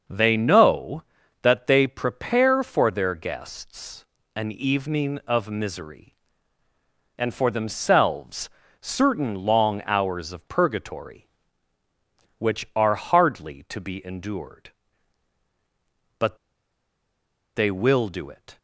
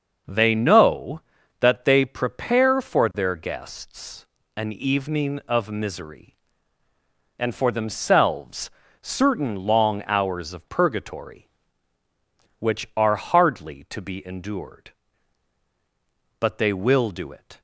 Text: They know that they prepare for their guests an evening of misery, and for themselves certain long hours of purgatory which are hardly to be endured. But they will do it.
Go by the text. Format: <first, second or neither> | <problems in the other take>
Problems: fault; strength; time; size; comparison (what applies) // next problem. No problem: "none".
second | starts louder than the rest; noticeable; until 1.4 s; 6 dB; noticeable in the second // pauses between "guests" and "an"; slight; at 4.0 s; 0.30 s long; slight in the second // pauses between "themselves" and "certain"; slight; at 8.4 s; 0.32 s long; slight in the second // pauses between "But" and "they"; at 16.3 s; 1.1 s long